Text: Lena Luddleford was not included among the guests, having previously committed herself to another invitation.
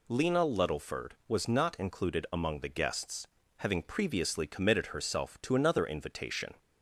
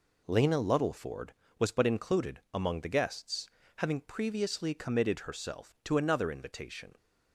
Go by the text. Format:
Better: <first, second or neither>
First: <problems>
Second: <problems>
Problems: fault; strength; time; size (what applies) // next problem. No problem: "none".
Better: first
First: none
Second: says "but" for "not"; at 1.7 s